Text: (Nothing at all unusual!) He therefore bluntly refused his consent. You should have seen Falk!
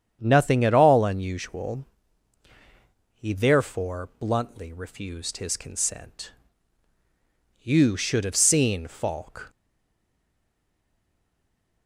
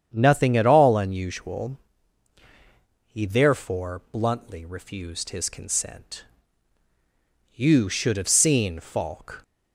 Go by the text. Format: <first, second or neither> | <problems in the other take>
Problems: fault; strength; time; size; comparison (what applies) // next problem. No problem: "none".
second | starts louder than the rest; strong; until 1.2 s; 8.5 dB; strong in the second // stays silent after the last word; from 9.4 s on; 2.4 s long